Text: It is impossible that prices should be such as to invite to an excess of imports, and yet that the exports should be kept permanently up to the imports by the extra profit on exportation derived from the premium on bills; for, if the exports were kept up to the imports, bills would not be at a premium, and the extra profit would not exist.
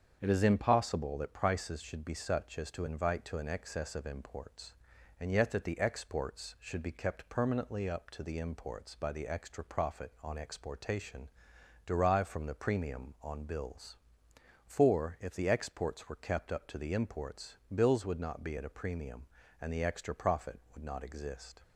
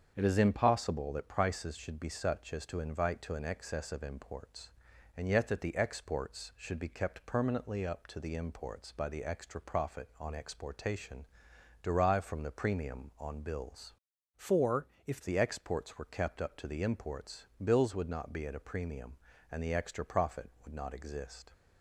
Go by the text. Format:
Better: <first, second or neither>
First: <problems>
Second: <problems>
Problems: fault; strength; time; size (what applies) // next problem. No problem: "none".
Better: first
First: starts louder than the rest; strong; until 1.2 s; 7.5 dB // pauses between "exportation" and "derived"; noticeable; at 11.2 s; 0.58 s long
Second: starts louder than the rest; strong; until 1.1 s; 7.5 dB // pauses between "exportation" and "derived"; noticeable; at 11.2 s; 0.58 s long // changes voice from "for" to "if"; from 14.3 to 15.2 s; 0.9 s long